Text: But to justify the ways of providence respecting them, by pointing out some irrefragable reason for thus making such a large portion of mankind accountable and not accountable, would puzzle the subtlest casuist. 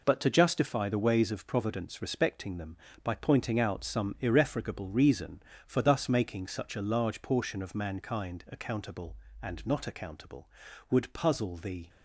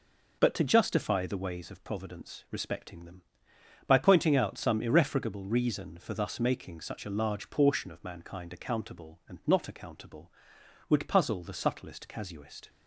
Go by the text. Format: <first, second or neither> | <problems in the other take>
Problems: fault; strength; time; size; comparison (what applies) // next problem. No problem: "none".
second | stops before "subtlest casuist"; at 11.8 s